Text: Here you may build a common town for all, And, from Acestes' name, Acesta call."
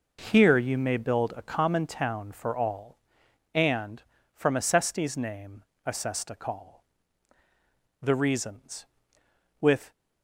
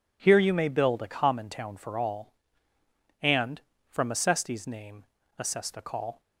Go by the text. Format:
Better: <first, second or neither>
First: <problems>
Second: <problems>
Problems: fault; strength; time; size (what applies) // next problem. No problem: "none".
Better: second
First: goes on to say "The reasons with"; strong; from 8.0 s on; 1.9 s long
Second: none